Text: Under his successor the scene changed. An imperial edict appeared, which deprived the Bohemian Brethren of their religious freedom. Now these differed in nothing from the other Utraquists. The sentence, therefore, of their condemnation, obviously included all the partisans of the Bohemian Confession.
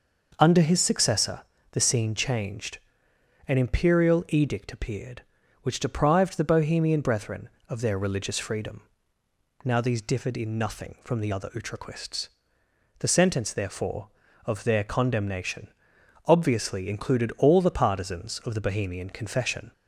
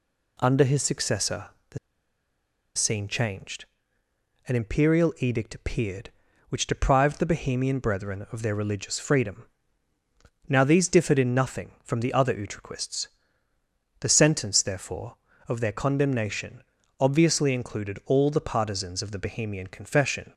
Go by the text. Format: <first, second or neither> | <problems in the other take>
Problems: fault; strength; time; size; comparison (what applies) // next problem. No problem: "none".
first | pauses between "successor" and "the"; slight; at 1.4 s; 0.22 s long; slight in the first // pauses between "the" and "scene"; at 1.7 s; 0.99 s long